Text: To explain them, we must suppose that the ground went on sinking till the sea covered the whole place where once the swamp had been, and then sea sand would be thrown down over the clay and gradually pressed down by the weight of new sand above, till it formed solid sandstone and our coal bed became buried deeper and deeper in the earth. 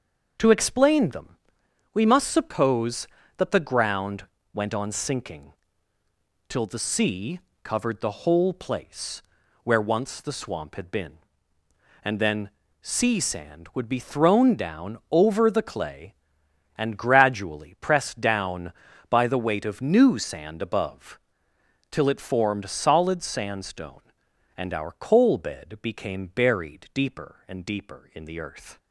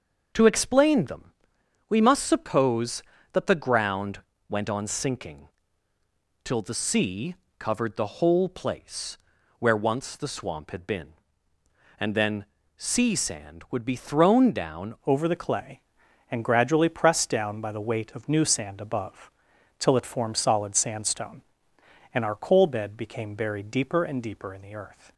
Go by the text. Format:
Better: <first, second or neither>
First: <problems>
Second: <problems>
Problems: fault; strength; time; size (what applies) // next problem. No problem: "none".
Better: first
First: starts louder than the rest; until 1.9 s; 6.5 dB // pauses between "ground" and "went"; slight; at 4.2 s; 0.28 s long // pauses between "sinking" and "till"; noticeable; at 5.5 s; 0.96 s long // pauses between "sea" and "covered"; slight; at 7.3 s; 0.24 s long // pauses between "place" and "where"; at 9.2 s; 0.42 s long // pauses between "then" and "sea"; slight; at 12.4 s; 0.32 s long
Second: starts louder than the rest; until 1.9 s; 6.5 dB // pauses between "ground" and "went"; slight; at 4.2 s; 0.28 s long // pauses between "sinking" and "till"; noticeable; at 5.4 s; 0.96 s long // pauses between "sea" and "covered"; slight; at 7.3 s; 0.24 s long // pauses between "place" and "where"; at 9.1 s; 0.42 s long // pauses between "then" and "sea"; slight; at 12.4 s; 0.32 s long // changes voice at "over"; from 15.0 s on; 10.1 s long